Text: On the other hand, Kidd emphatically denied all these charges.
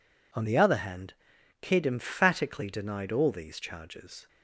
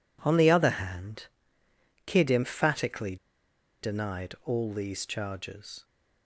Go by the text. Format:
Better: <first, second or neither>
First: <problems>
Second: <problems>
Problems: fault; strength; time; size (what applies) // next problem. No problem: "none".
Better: first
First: none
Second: pauses between "emphatically" and "denied"; noticeable; at 3.1 s; 0.65 s long